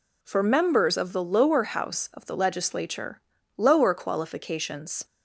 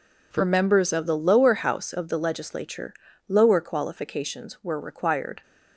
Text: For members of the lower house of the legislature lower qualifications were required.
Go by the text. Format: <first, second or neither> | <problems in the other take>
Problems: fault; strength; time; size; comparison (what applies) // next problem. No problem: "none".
second | pauses between "legislature" and "lower"; slight; at 3.2 s; 0.36 s long; slight in the second // stops before "were required"; at 5.0 s